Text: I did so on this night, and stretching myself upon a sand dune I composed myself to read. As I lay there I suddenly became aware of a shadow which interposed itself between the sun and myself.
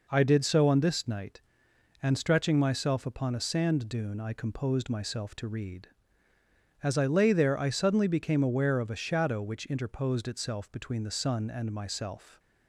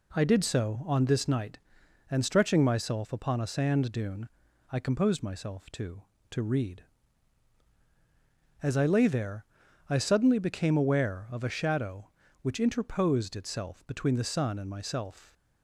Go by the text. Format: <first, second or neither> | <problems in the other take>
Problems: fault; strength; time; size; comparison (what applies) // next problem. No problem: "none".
first | pauses between "dune" and "I"; at 4.2 s; 0.42 s long // says "to" twice; at 6.3 s // pauses between "there" and "I"; at 9.4 s; 0.44 s long